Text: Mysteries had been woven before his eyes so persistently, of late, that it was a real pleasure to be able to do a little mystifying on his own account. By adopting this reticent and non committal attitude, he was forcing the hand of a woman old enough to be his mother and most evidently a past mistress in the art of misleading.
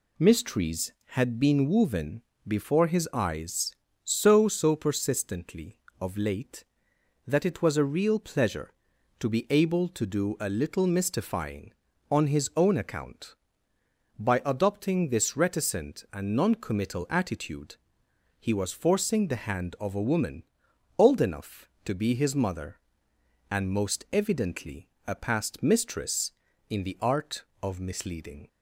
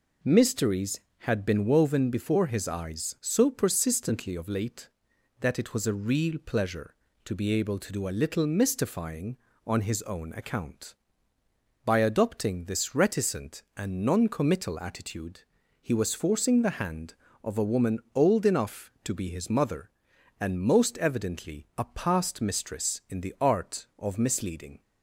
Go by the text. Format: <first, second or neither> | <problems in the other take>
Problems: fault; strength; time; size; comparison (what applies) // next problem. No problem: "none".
second | pauses between "woven" and "before"; slight; at 2.2 s; 0.26 s long // says "so" twice; at 4.4 s // pauses between "woman" and "old"; noticeable; at 20.4 s; 0.54 s long; slight in the second // pauses between "evidently" and "a"; slight; at 24.8 s; 0.18 s long